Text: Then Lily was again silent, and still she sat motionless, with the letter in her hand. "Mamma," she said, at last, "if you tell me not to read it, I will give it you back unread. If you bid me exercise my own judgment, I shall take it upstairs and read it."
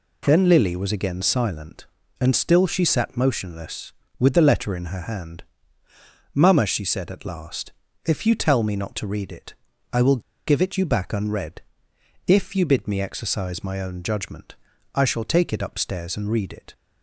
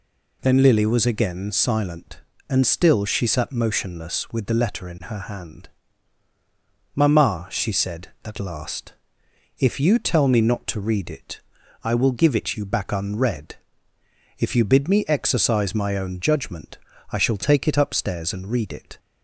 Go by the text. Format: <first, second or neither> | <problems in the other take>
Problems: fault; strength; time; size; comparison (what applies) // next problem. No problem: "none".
second | pauses between "will" and "give"; slight; at 10.2 s; 0.26 s long